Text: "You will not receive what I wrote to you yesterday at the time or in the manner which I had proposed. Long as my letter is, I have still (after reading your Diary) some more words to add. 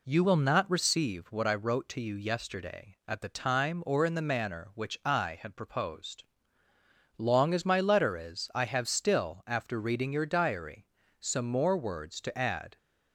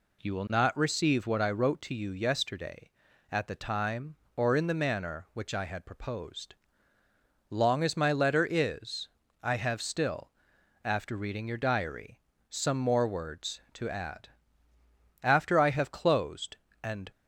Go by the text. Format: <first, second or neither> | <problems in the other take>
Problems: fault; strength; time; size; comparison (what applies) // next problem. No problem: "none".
first | goes on to say "After I have closed and"; strong; from 15.2 s on; 1.8 s long